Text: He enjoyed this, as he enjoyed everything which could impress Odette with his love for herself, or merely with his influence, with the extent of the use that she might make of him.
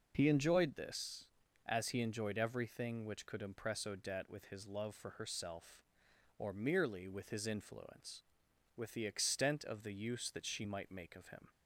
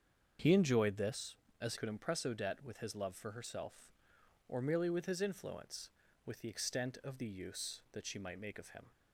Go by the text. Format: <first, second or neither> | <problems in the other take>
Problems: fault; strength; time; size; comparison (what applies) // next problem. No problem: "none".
first | starts louder than the rest; strong; until 1.6 s; 7.5 dB // skips "he enjoyed everything which"; at 1.7 s